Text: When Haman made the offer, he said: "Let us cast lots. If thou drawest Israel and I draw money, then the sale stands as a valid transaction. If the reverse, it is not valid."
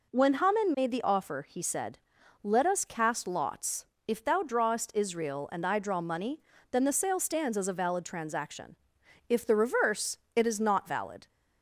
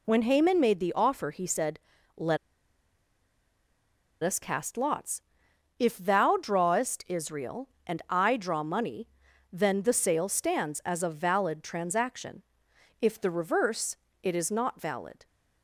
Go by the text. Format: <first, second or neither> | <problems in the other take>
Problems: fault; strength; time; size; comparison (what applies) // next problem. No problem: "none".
first | pauses between "Let" and "us"; strong; at 2.3 s; 1.8 s long